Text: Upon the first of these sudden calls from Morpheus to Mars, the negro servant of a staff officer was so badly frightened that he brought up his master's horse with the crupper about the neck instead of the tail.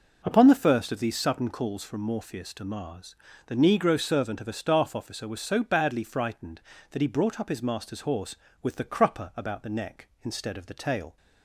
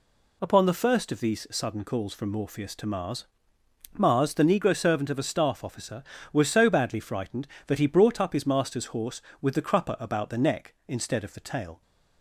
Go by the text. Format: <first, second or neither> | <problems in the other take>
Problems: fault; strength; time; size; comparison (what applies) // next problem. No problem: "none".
first | says "Mars" twice; at 3.9 s